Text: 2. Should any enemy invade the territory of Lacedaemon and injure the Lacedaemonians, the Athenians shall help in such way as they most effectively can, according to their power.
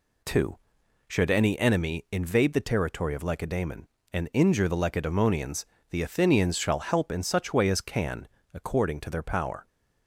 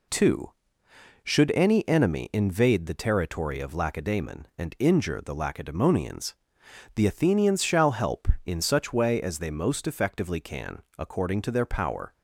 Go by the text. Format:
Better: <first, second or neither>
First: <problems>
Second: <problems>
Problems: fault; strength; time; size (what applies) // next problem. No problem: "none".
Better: second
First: skips "they most effectively"; at 7.8 s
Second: none